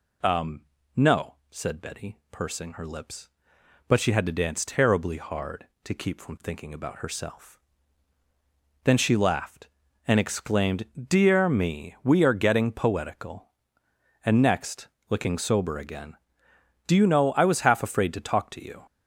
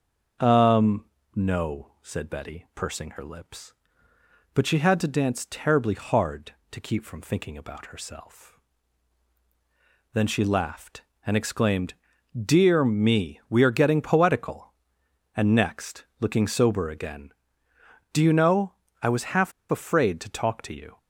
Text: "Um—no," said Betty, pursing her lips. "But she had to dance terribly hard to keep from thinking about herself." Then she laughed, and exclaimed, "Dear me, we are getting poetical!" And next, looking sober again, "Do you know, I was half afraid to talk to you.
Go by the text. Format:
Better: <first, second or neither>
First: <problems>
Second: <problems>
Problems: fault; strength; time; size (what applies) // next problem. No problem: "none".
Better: first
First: none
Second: starts louder than the rest; until 1.6 s; 6.5 dB // pauses between "half" and "afraid"; slight; at 19.5 s; 0.17 s long